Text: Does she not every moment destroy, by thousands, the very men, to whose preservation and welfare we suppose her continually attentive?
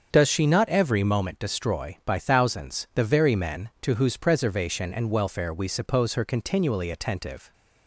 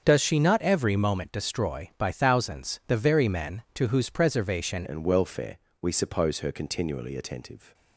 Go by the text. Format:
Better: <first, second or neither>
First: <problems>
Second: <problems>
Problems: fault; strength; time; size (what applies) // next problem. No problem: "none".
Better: first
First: starts louder than the rest; until 1.1 s; 7 dB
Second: starts louder than the rest; until 1.0 s; 7 dB // changes voice at "and"; from 4.8 s on; 2.9 s long // pauses between "welfare" and "we"; slight; at 5.5 s; 0.22 s long